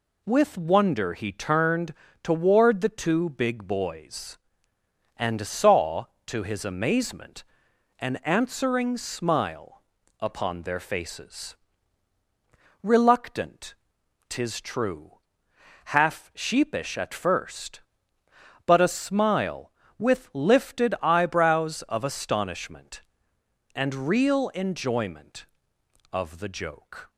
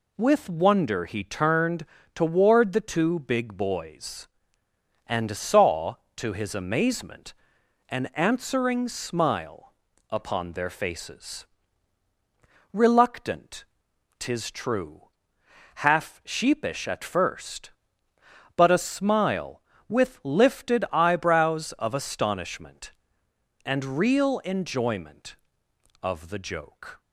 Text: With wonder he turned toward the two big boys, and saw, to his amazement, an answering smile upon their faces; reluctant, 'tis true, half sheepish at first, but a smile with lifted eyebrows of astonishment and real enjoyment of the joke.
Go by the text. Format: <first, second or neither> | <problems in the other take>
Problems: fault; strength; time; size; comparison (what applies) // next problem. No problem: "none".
neither | pauses between "turned" and "toward"; slight; the same in both // pauses between "smile" and "upon"; the same in both